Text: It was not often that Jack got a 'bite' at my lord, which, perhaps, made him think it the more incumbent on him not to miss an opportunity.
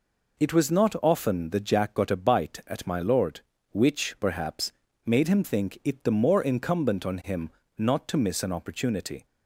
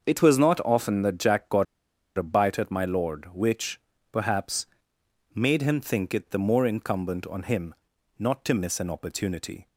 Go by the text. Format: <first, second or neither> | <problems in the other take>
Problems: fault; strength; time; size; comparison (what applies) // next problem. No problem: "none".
first | starts louder than the rest; until 1.0 s; 6.5 dB // pauses between "got" and "a"; noticeable; at 1.6 s; 0.53 s long // pauses between "him" and "not"; noticeable; at 7.7 s; 0.46 s long; slight in the first